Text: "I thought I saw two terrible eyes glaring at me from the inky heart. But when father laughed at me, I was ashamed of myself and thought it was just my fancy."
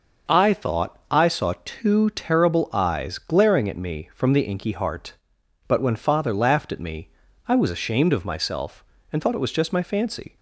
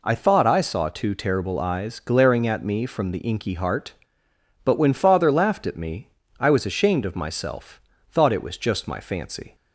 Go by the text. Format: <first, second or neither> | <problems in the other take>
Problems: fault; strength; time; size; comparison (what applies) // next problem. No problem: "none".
first | skips "and"; at 7.9 s